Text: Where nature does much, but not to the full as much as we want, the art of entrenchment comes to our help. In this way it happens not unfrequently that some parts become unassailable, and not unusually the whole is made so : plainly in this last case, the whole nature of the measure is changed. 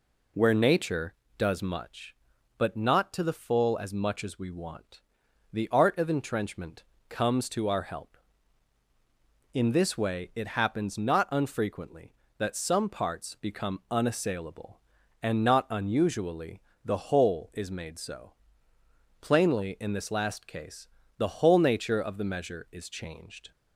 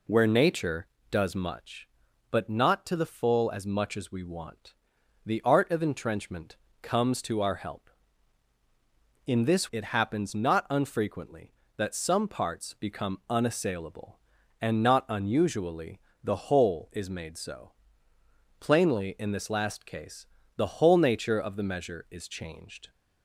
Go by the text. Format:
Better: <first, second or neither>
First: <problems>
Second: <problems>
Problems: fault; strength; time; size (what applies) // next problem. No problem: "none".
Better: first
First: pauses between "entrenchment" and "comes"; slight; at 6.8 s; 0.26 s long // pauses between "unusually" and "the"; slight; at 16.6 s; 0.22 s long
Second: pauses between "entrenchment" and "comes"; slight; at 6.5 s; 0.26 s long // skips "way"; at 9.7 s // pauses between "unusually" and "the"; slight; at 15.9 s; 0.22 s long